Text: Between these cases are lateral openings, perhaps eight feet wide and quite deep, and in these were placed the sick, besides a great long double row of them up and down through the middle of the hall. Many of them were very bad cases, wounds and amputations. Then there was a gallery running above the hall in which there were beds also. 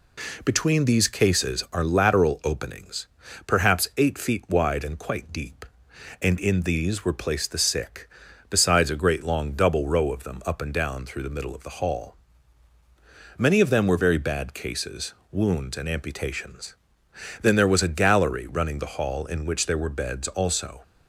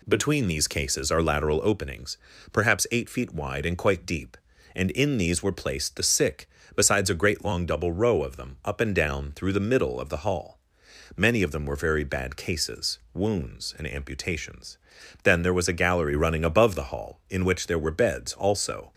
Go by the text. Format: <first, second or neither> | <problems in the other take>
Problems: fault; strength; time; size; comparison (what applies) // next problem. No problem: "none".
second | skips "above"; at 18.7 s